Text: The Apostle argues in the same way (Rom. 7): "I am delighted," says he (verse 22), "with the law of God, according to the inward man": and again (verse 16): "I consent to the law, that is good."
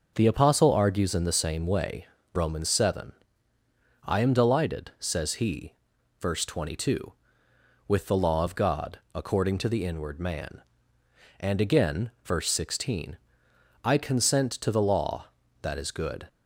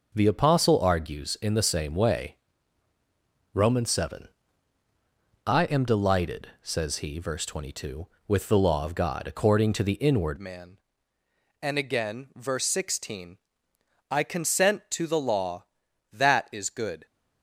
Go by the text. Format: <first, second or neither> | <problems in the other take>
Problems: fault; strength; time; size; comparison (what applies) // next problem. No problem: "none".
first | changes voice at "man"; from 10.3 s on; 6.7 s long